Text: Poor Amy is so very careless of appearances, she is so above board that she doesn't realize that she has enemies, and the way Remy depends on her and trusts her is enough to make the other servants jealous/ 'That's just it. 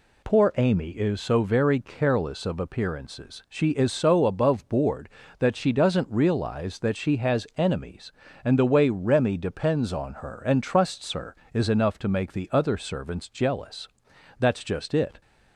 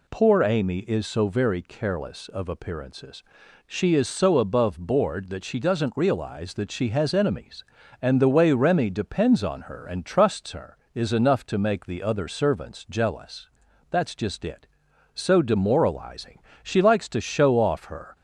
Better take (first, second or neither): first